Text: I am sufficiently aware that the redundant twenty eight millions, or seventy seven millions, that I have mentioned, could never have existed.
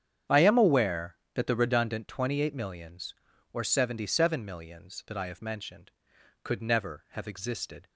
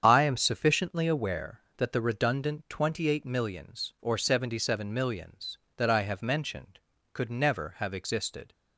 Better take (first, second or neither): second